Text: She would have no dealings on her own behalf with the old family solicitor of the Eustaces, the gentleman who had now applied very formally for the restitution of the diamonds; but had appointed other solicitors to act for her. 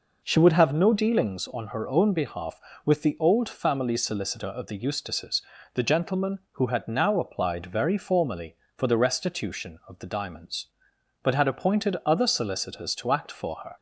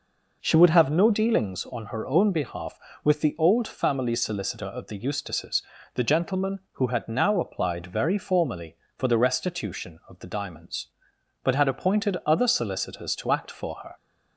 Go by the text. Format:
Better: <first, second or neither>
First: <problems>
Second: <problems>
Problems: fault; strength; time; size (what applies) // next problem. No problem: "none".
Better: neither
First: none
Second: none